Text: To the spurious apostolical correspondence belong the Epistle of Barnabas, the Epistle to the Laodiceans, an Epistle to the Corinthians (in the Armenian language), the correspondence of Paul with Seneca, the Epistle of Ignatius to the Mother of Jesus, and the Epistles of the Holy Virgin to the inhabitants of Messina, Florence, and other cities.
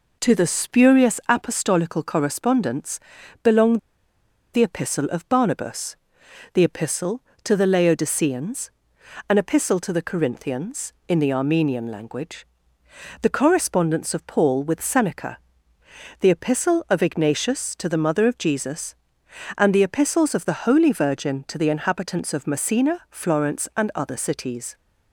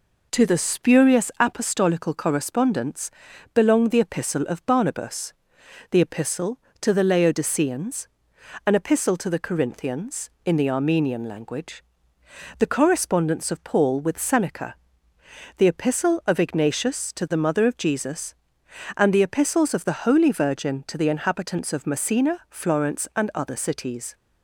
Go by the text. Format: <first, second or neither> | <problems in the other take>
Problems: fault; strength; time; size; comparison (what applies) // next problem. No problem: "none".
second | pauses between "correspondence" and "belong"; at 2.9 s; 0.44 s long; also in the second // pauses between "belong" and "the"; noticeable; at 3.7 s; 0.76 s long